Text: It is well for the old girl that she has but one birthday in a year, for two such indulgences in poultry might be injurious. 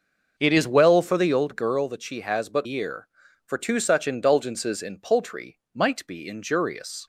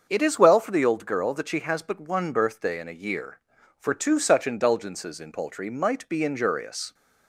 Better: second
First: starts louder than the rest; noticeable; until 1.3 s; 6 dB // skips "one birthday in a"; at 2.6 s // pauses between "poultry" and "might"; slight; at 5.5 s; 0.16 s long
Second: starts louder than the rest; until 1.1 s; 6.5 dB

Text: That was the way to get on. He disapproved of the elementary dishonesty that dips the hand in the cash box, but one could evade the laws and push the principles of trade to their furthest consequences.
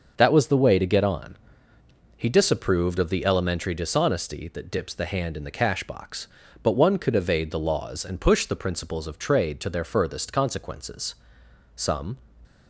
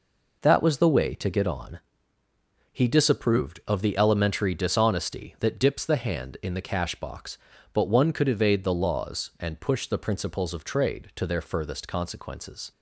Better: second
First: goes on to say "Some"; slight; from 11.7 s on; 0.42 s long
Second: none

